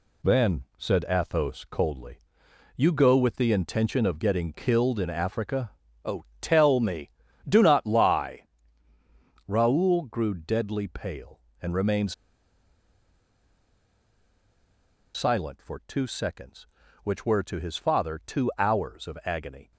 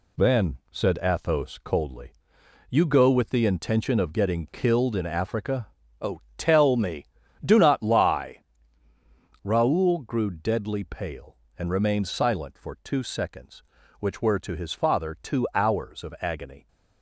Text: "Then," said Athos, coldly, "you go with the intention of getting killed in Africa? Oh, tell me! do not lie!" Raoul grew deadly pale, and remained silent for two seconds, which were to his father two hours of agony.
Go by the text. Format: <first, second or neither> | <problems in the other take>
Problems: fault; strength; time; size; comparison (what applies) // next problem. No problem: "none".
second | pauses between "remained" and "silent"; strong; at 12.1 s; 3.0 s long